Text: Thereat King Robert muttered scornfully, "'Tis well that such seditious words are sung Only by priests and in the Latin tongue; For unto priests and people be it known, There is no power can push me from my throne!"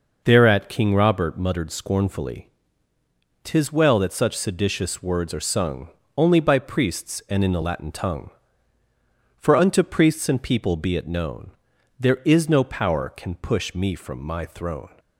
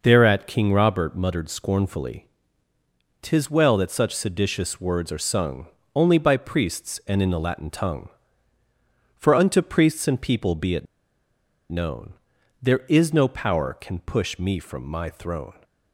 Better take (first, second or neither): first